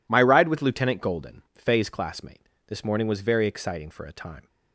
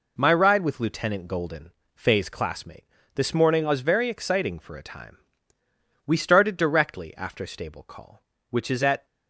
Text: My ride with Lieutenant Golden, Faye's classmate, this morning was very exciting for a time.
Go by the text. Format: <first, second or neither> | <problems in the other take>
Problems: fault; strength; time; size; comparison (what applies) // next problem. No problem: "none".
first | goes on to say "We started directly after stable call which is at"; strong; from 6.0 s on; 3.0 s long